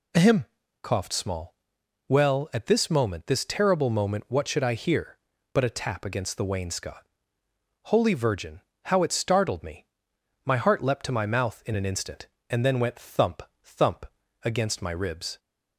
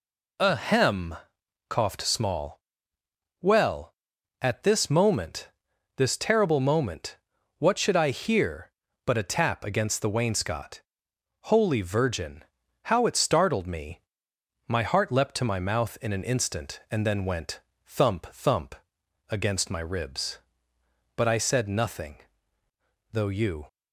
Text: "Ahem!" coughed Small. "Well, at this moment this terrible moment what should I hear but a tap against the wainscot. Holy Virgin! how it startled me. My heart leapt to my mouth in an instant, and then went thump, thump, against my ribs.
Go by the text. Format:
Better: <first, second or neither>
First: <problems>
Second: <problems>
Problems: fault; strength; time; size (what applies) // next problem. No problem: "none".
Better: first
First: none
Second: pauses between "moment" and "this"; noticeable; at 5.4 s; 0.46 s long // pauses between "moment" and "what"; at 7.1 s; 0.42 s long // pauses between "went" and "thump"; slight; at 17.6 s; 0.24 s long // goes on to say "But I said nothing though you"; strong; from 21.1 s on; 2.5 s long